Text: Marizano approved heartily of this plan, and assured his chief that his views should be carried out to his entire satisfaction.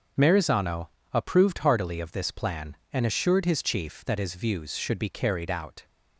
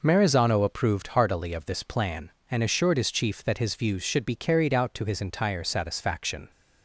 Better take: second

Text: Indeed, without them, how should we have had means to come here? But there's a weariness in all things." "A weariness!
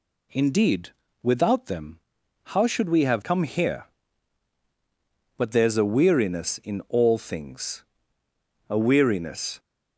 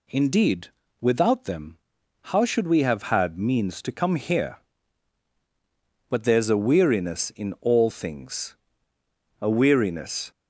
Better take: second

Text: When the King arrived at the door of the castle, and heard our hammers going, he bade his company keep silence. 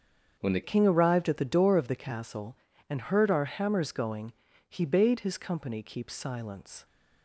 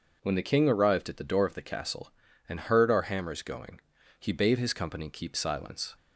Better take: second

